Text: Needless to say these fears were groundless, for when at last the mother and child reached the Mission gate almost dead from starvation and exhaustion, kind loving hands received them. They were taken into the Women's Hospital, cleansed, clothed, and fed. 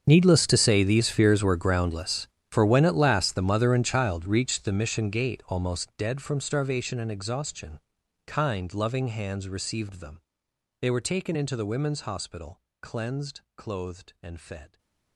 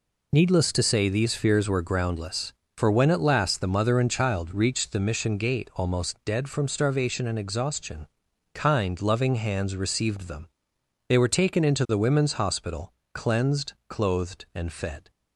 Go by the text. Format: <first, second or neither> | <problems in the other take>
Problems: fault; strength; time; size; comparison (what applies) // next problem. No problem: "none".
second | gets quieter; strong; throughout; 20 dB